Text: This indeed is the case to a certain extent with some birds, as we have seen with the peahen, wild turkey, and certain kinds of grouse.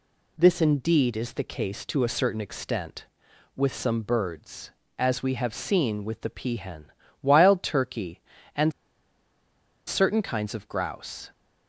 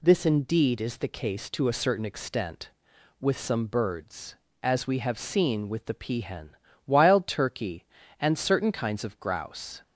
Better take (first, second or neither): second